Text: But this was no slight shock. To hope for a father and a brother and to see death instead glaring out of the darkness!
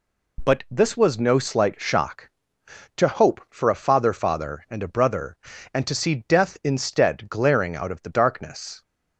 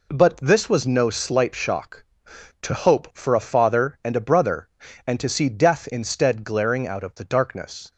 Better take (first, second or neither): second